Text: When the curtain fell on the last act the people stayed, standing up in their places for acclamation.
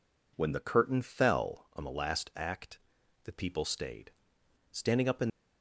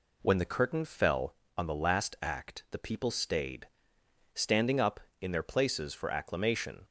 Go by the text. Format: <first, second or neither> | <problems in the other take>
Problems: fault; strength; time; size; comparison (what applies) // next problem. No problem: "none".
second | pauses between "act" and "the"; noticeable; at 2.7 s; 0.46 s long // stops before "their places for acclamation"; at 5.2 s